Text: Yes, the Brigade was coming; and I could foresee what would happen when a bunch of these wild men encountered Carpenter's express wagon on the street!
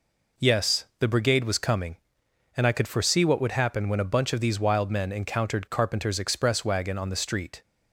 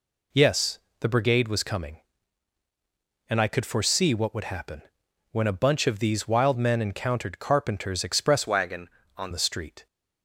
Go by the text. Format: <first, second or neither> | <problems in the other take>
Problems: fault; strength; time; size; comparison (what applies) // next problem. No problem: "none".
first | pauses between "happen" and "when"; noticeable; at 4.8 s; 0.50 s long // changes voice from "wagon" to "on"; from 8.4 to 9.3 s; 0.9 s long